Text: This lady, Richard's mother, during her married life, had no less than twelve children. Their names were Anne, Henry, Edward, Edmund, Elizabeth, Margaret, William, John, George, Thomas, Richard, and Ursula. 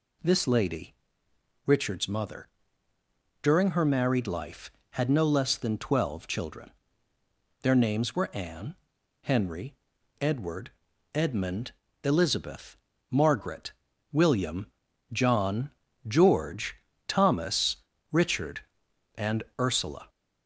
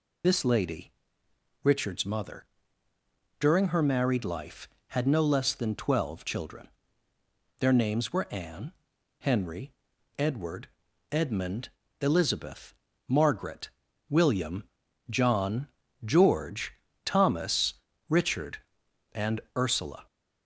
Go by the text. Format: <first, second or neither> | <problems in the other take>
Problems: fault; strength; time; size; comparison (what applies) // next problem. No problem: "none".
first | loses the start of "This"; at 0.2 s; 65 ms